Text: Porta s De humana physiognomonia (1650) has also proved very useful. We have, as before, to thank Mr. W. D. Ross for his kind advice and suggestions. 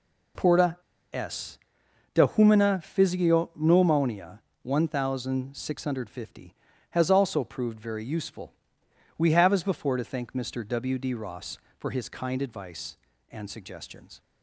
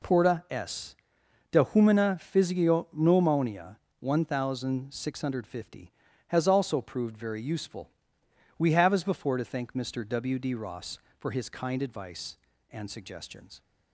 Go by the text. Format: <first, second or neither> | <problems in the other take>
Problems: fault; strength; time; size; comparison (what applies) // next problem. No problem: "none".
second | pauses between "Porta" and "s"; at 0.7 s; 0.37 s long // pauses between "s" and "De"; noticeable; at 1.5 s; 0.56 s long; noticeable in the second